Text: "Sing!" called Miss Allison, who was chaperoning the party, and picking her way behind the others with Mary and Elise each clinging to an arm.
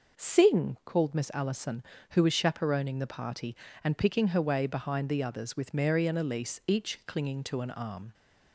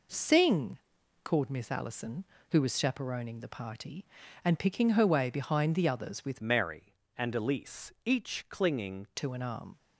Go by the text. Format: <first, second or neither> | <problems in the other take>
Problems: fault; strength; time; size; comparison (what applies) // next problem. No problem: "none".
first | changes voice from "Mary" to "clinging"; from 6.3 to 9.0 s; 2.7 s long